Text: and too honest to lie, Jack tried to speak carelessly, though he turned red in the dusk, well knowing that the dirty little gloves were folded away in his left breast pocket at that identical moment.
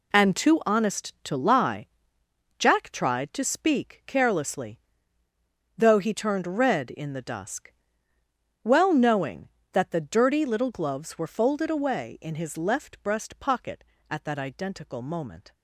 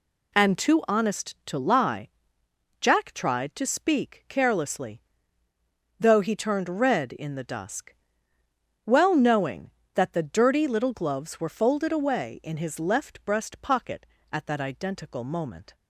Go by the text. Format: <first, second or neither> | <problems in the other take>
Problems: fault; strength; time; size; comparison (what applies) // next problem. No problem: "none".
second | gets quieter; strong; throughout; 12 dB